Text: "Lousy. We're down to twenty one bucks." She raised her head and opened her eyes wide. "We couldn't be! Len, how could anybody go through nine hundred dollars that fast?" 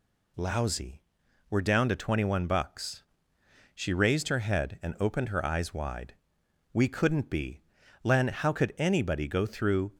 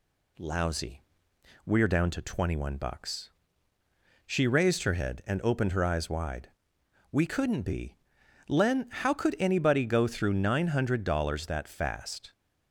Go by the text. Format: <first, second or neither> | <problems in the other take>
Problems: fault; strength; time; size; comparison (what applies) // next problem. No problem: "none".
second | stops before "nine hundred dollars that fast"; at 9.9 s